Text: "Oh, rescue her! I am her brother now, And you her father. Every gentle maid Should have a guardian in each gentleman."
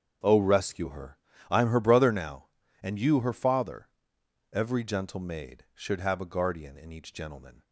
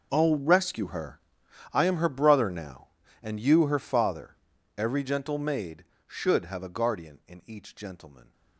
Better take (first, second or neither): first